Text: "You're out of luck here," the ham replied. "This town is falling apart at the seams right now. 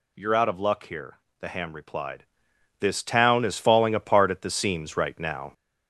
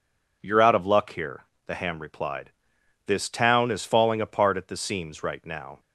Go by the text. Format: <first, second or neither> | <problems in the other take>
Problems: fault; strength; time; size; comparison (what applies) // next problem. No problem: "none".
second | gets louder; noticeable; throughout; 5.5 dB